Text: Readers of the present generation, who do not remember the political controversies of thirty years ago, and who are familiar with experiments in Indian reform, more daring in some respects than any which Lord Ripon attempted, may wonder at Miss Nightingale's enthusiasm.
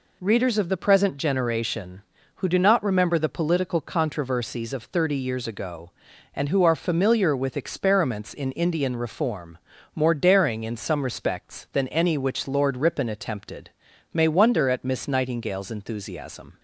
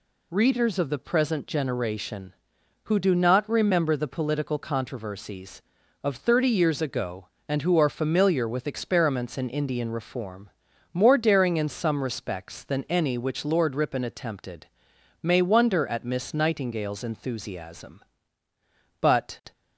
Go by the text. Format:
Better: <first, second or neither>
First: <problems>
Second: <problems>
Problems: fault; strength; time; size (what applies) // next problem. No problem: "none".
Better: first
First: none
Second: goes on to say "But"; from 18.9 s on; 0.52 s long